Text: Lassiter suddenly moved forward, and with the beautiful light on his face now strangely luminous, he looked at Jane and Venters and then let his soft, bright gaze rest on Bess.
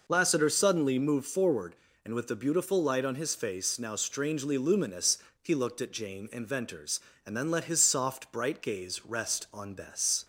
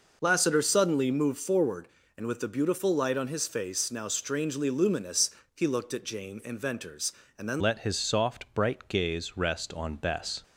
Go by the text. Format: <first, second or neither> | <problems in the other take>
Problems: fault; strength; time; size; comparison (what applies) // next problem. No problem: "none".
first | changes voice at "let"; from 7.6 s on; 2.8 s long